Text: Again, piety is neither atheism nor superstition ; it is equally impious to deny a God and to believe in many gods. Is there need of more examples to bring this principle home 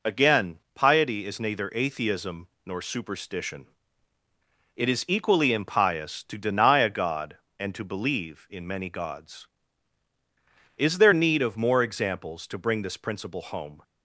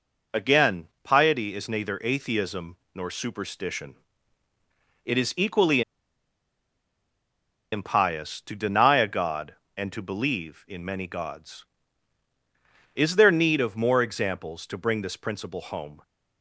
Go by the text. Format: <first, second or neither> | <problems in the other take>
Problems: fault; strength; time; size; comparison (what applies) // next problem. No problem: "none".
first | pauses between "atheism" and "nor"; slight; at 2.7 s; 0.18 s long; slight in the first // pauses between "equally" and "impious"; strong; at 5.8 s; 1.9 s long